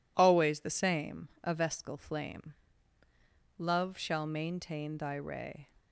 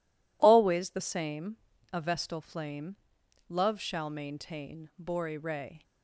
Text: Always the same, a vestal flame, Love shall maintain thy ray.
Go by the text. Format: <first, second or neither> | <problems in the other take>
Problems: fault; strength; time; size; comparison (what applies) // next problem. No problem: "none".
first | says "bori" for "thy"; at 4.9 s